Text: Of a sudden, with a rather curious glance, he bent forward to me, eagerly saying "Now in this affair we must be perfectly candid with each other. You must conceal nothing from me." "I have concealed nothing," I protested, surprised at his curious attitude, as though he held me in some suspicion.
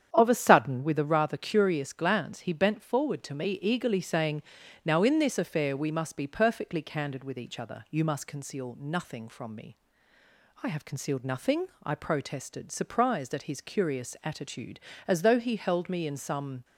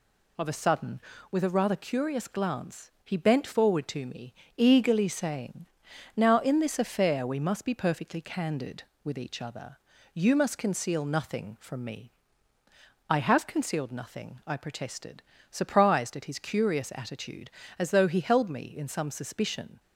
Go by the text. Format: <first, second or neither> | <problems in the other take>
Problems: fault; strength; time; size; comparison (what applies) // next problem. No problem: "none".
second | starts louder than the rest; strong; until 1.1 s; 9 dB // pauses between "saying" and "Now"; at 4.4 s; 0.42 s long; noticeable in the second // stops before "suspicion"; at 16.6 s